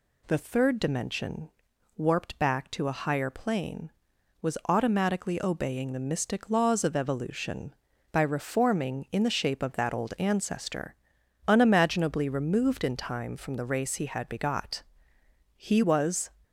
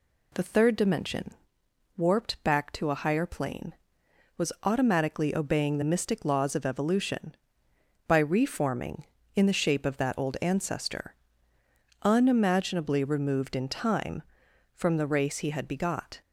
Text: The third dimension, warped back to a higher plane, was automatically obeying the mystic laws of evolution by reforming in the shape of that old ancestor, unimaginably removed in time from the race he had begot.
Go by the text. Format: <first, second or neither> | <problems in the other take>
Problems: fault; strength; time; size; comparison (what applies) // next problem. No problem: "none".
second | goes on to say "He was"; noticeable; from 15.5 s on; 0.74 s long